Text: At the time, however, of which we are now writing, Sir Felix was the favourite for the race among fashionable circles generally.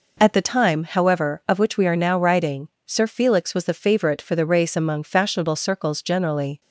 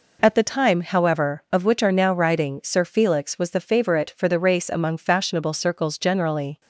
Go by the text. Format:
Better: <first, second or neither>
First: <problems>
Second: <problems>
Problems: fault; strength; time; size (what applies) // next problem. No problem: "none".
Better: first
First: none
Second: skips "we"; at 1.8 s